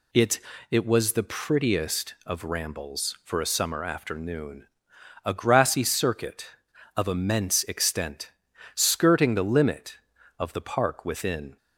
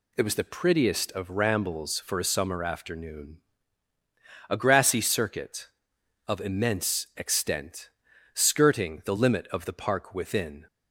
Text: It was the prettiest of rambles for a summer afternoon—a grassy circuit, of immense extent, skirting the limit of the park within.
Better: second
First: says "It" twice; at 0.6 s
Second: none

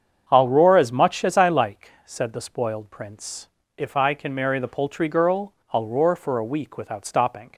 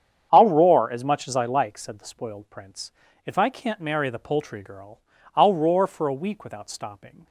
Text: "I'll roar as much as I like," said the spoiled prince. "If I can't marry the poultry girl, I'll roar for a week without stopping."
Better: second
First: starts louder than the rest; strong; until 1.2 s; 7.5 dB // says "can" for "can't"; at 4.1 s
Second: starts louder than the rest; strong; until 1.3 s; 8 dB

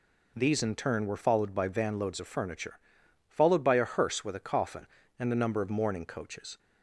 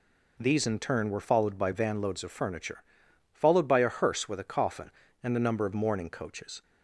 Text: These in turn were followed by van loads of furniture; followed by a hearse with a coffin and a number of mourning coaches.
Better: neither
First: none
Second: none

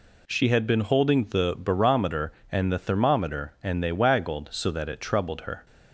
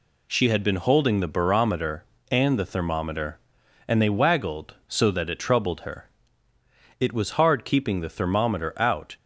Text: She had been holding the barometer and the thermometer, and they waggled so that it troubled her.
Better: first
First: none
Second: goes on to say "It was hard keeping the thermometer out"; strong; from 6.9 s on; 2.1 s long

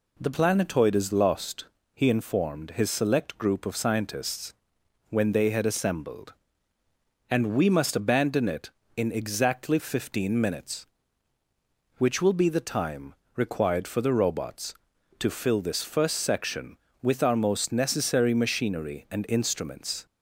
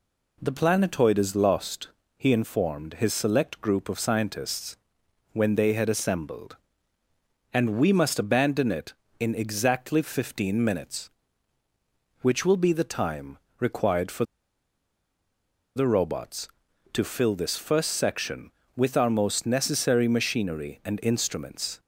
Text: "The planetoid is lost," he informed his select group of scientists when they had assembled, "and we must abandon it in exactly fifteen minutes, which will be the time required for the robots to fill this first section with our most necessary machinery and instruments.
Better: first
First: pauses between "scientists" and "when"; noticeable; at 4.5 s; 0.56 s long // pauses between "time" and "required"; slight; at 13.1 s; 0.22 s long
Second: pauses between "scientists" and "when"; noticeable; at 4.7 s; 0.56 s long // pauses between "time" and "required"; slight; at 13.3 s; 0.22 s long // pauses between "for" and "the"; strong; at 14.2 s; 1.5 s long

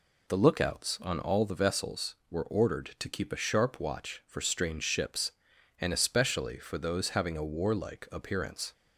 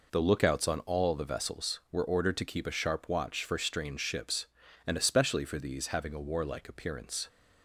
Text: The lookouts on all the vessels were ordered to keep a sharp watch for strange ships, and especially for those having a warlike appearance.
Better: first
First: none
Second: says "these" for "those"; at 5.5 s

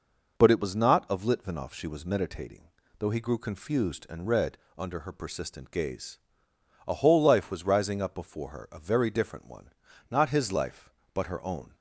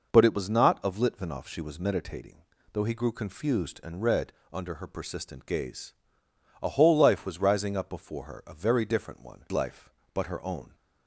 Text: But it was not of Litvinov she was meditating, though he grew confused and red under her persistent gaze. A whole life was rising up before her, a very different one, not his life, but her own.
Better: first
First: pauses between "red" and "under"; slight; at 4.5 s; 0.20 s long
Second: pauses between "red" and "under"; slight; at 4.3 s; 0.20 s long // skips "not his"; at 9.4 s

